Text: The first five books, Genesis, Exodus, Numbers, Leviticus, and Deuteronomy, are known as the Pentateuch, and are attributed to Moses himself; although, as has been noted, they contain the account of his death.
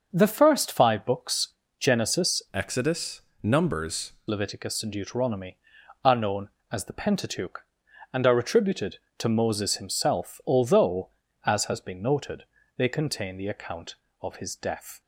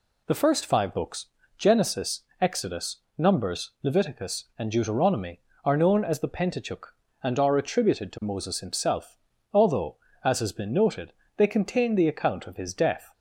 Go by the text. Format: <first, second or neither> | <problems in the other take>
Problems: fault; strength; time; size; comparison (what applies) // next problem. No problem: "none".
second | starts louder than the rest; until 1.1 s; 6 dB // changes voice from "Exodus" to "Numbers"; from 2.5 to 4.1 s; 1.6 s long